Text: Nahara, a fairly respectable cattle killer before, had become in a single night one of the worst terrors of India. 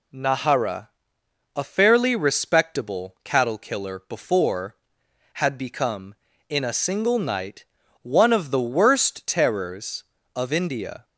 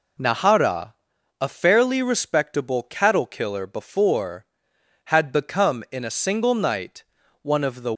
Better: first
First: pauses between "night" and "one"; at 7.6 s; 0.38 s long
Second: pauses between "night" and "one"; at 7.0 s; 0.40 s long // stops before "worst terrors of India"; at 7.9 s

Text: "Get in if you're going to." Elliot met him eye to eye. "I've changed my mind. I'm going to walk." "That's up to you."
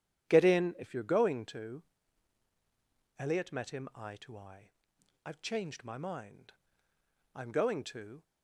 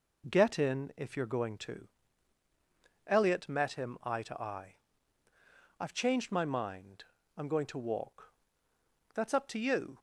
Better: second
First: starts louder than the rest; strong; until 1.3 s; 9.5 dB // stops before "walk That's up to you"; at 8.2 s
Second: none

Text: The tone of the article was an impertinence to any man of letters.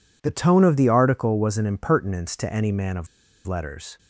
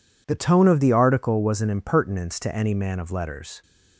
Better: second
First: pauses between "of" and "letters"; at 3.0 s; 0.38 s long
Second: none

